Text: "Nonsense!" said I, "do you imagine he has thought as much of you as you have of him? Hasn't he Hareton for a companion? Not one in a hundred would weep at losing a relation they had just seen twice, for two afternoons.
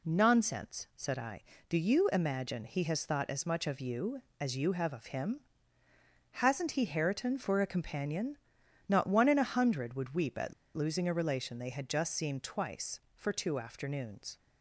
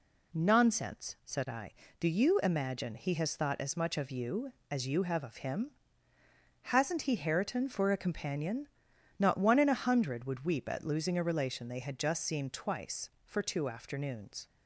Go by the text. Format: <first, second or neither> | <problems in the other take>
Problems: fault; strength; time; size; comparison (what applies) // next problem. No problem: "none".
second | pauses between "at" and "losing"; slight; at 10.5 s; 0.23 s long